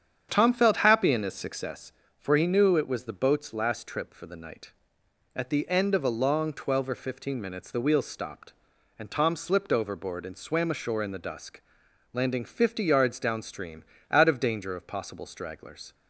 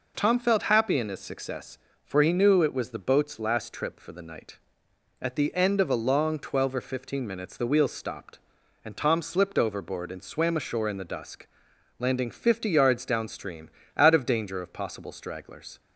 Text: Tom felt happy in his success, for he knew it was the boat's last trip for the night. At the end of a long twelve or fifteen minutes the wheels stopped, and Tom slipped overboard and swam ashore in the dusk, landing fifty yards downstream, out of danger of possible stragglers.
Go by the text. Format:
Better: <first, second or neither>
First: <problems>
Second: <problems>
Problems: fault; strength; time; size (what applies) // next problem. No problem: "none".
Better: second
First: starts louder than the rest; strong; until 1.7 s; 8.5 dB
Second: none